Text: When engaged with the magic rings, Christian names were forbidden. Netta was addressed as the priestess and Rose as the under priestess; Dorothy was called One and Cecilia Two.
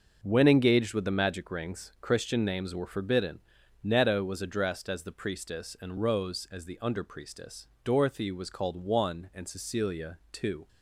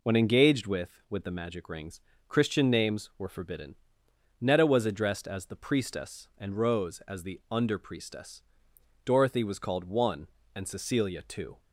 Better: first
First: none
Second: says "with" twice; at 1.1 s

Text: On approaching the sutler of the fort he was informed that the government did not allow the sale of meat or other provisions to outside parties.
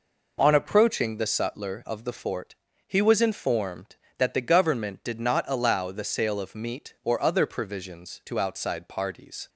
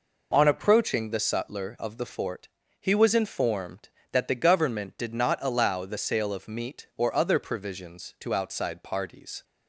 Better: neither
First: pauses between "fort" and "he"; slight; at 2.5 s; 0.32 s long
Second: pauses between "fort" and "he"; slight; at 2.4 s; 0.32 s long

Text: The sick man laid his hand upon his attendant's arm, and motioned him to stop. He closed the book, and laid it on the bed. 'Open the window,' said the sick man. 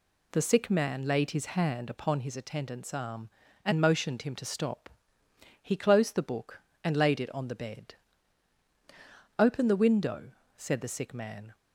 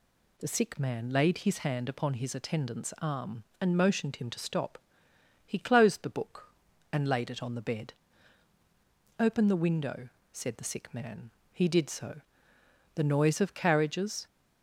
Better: first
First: none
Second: goes on to say "He did so The noise of carriages"; strong; from 11.5 s on; 2.7 s long

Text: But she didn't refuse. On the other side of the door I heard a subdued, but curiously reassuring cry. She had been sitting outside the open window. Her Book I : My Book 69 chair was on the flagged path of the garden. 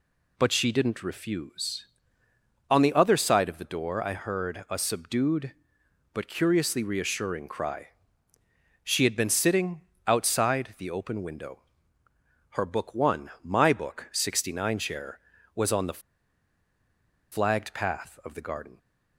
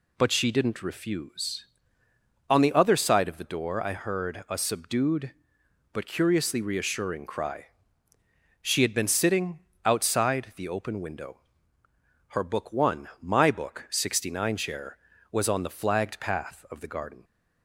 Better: second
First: pauses between "sitting" and "outside"; slight; at 9.8 s; 0.24 s long // pauses between "the" and "flagged"; strong; at 15.9 s; 1.3 s long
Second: pauses between "sitting" and "outside"; slight; at 9.5 s; 0.24 s long

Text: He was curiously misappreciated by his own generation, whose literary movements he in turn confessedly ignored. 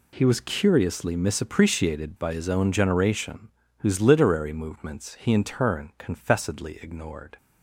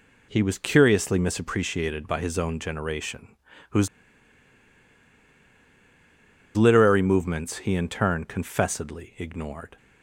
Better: first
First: none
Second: pauses between "whose" and "literary"; strong; at 3.8 s; 2.6 s long

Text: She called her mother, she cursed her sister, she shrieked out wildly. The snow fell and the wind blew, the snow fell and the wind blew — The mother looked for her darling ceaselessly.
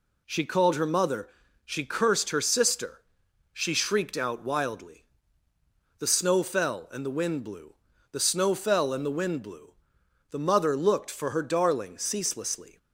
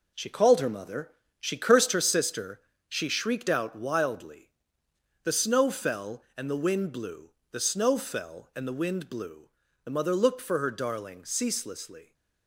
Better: first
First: none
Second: gets quieter; throughout; 7 dB

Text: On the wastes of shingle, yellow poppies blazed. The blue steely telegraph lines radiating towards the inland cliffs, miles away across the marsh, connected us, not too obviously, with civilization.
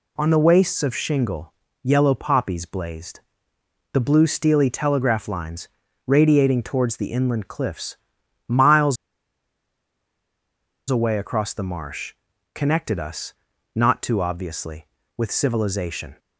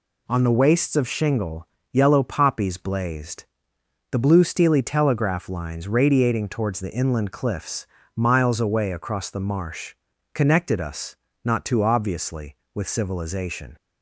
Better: second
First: pauses between "lines" and "radiating"; at 5.6 s; 0.38 s long // pauses between "miles" and "away"; strong; at 8.9 s; 1.9 s long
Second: none

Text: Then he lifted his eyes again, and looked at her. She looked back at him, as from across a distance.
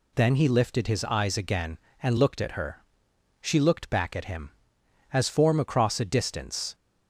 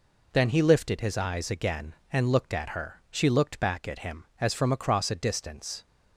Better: second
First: says "form" for "from"; at 5.2 s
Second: none

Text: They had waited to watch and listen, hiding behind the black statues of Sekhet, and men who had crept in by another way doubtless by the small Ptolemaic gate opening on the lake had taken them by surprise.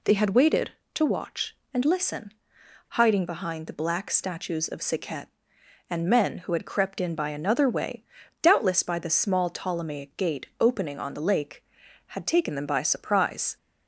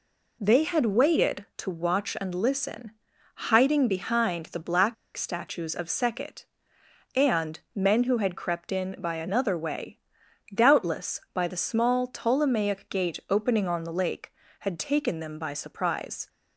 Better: first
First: pauses between "way" and "doubtless"; at 8.0 s; 0.40 s long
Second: pauses between "black" and "statues"; slight; at 4.9 s; 0.21 s long // pauses between "and" and "men"; slight; at 7.5 s; 0.16 s long // pauses between "way" and "doubtless"; noticeable; at 9.9 s; 0.56 s long

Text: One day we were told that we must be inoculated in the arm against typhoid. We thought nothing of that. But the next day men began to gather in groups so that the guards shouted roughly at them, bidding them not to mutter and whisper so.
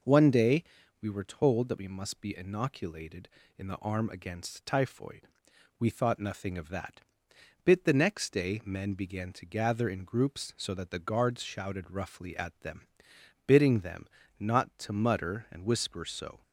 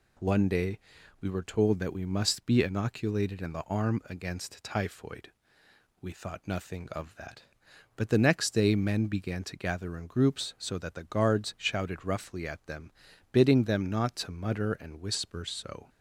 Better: second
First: pauses between "day" and "we"; slight; at 0.6 s; 0.36 s long // says "Bit" for "But"; at 7.6 s // pauses between "them" and "not"; slight; at 14.0 s; 0.32 s long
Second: pauses between "day" and "we"; at 0.7 s; 0.42 s long

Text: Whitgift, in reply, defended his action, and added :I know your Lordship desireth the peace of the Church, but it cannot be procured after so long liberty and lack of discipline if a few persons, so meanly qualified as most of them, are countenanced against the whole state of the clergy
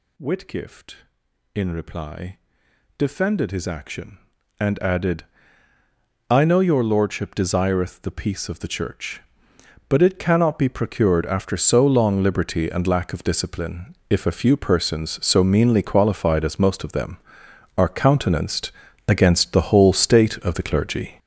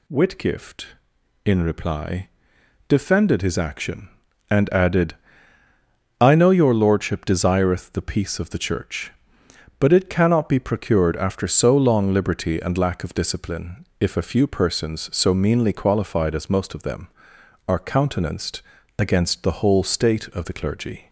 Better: second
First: gets louder; strong; throughout; 9 dB // pauses between "countenanced" and "against"; at 18.7 s; 0.38 s long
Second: pauses between "countenanced" and "against"; at 18.6 s; 0.38 s long

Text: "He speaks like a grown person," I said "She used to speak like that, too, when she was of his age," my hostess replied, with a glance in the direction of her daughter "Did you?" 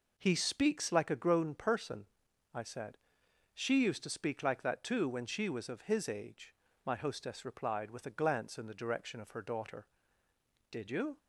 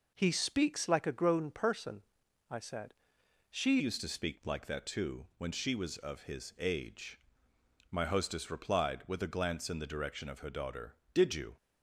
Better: first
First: pauses between "said" and "She"; noticeable; at 2.9 s; 0.56 s long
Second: pauses between "said" and "She"; noticeable; at 2.9 s; 0.56 s long // changes voice at "used"; from 3.7 s on; 7.8 s long

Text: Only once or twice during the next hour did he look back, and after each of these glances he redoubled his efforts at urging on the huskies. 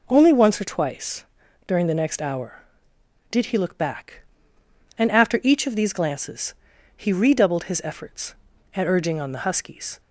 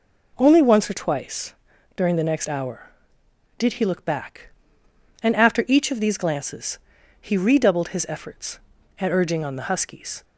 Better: neither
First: pauses between "twice" and "during"; at 1.2 s; 0.40 s long // pauses between "glances" and "he"; at 6.5 s; 0.42 s long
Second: pauses between "twice" and "during"; at 1.5 s; 0.40 s long // pauses between "glances" and "he"; at 6.7 s; 0.42 s long

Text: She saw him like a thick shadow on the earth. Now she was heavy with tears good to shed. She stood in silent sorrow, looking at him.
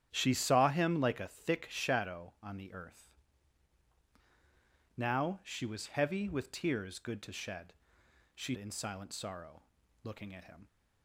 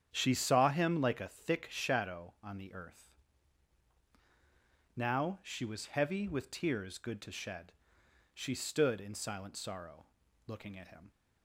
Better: second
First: starts louder than the rest; strong; until 1.1 s; 10.5 dB // skips "stood"; at 8.5 s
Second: starts louder than the rest; strong; until 1.1 s; 9 dB

